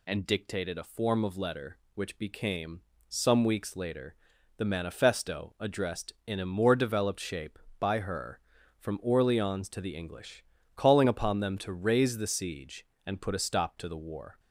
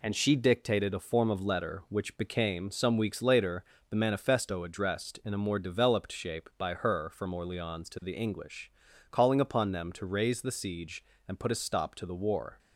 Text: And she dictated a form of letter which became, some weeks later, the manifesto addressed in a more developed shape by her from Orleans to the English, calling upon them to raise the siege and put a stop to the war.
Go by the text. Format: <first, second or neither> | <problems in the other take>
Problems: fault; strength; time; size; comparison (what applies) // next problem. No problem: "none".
second | skips "she"; at 0.2 s